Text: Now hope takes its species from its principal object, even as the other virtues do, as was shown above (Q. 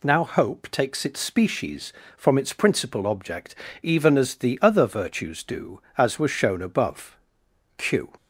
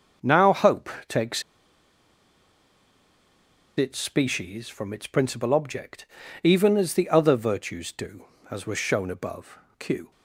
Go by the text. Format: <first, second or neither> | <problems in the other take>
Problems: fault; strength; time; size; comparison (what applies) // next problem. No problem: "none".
first | starts louder than the rest; until 1.4 s; 6.5 dB // pauses between "hope" and "takes"; slight; at 0.8 s; 0.18 s long // pauses between "takes" and "its"; strong; at 1.4 s; 2.3 s long